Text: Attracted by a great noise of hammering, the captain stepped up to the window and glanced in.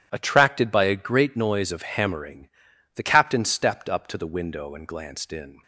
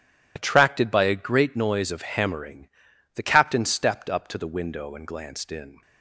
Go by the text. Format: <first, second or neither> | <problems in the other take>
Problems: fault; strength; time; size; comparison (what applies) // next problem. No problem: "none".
first | loses the start of "Attracted"; at 0.3 s; 40 ms